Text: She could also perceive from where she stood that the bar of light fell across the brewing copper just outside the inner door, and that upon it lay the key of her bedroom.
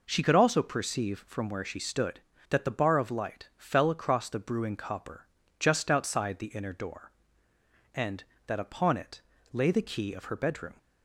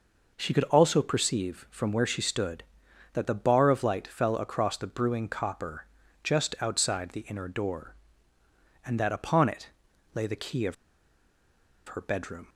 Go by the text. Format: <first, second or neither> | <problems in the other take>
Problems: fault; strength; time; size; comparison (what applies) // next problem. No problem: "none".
first | pauses between "copper" and "just"; at 5.8 s; 0.38 s long; slight in the first // pauses between "it" and "lay"; at 9.6 s; 0.44 s long; slight in the first // pauses between "of" and "her"; at 10.7 s; 1.1 s long